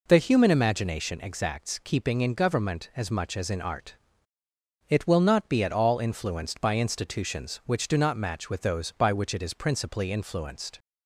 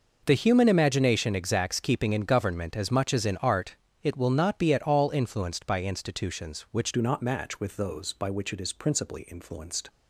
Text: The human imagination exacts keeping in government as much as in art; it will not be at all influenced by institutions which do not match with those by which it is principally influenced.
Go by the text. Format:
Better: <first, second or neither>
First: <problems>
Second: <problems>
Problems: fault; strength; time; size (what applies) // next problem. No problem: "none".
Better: first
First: none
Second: changes voice at "do"; from 6.9 s on; 2.9 s long